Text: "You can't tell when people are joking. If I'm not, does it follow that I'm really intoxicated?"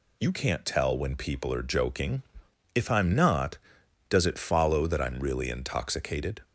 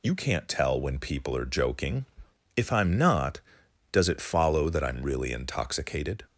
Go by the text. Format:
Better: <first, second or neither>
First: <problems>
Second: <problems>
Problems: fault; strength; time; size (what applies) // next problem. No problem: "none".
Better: neither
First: none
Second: none